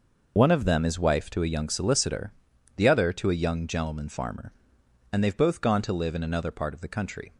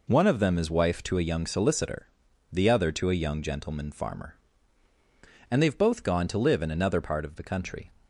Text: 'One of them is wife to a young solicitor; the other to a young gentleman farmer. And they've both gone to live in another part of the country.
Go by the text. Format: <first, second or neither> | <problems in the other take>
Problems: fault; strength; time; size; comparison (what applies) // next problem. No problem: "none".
second | loses the start of "One"; at 0.3 s; 40 ms